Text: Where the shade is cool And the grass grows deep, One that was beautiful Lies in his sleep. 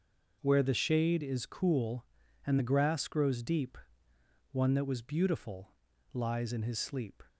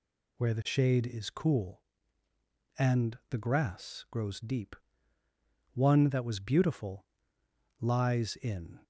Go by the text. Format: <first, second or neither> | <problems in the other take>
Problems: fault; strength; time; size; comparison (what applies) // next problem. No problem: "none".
first | pauses between "beautiful" and "Lies"; noticeable; at 7.0 s; 0.76 s long; also in the first // stops before "his sleep"; at 8.8 s